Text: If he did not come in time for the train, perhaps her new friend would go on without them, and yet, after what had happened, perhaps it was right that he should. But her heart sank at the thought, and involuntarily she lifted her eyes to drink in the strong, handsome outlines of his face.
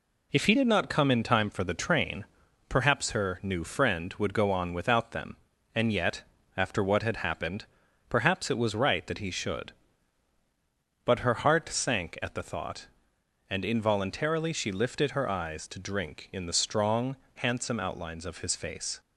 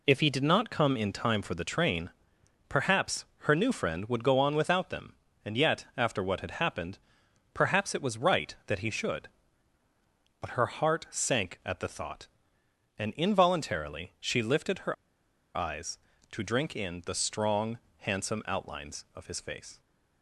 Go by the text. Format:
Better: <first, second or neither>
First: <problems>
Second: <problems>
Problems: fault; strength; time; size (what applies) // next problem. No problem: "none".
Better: first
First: none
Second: pauses between "perhaps" and "her"; slight; at 3.2 s; 0.16 s long // pauses between "her" and "eyes"; noticeable; at 14.9 s; 0.61 s long